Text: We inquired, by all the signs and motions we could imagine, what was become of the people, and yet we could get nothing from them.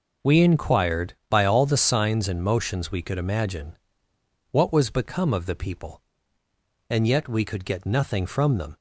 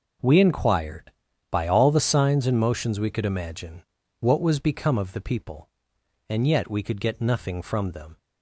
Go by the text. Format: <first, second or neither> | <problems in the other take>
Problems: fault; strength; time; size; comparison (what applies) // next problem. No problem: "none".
neither | none